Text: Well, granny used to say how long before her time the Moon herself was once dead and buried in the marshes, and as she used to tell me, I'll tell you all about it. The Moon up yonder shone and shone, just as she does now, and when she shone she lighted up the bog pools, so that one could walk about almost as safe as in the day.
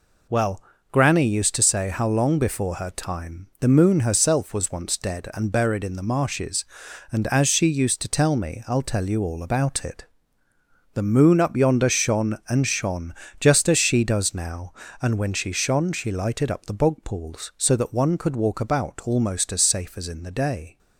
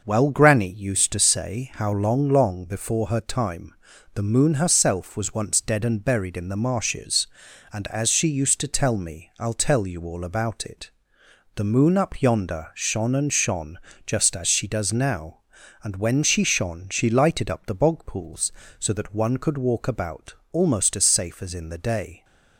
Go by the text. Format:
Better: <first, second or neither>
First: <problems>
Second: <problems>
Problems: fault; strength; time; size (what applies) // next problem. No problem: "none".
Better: first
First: none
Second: says "long" twice; at 2.2 s // pauses between "time" and "the"; at 3.7 s; 0.40 s long // pauses between "about" and "almost"; slight; at 20.3 s; 0.18 s long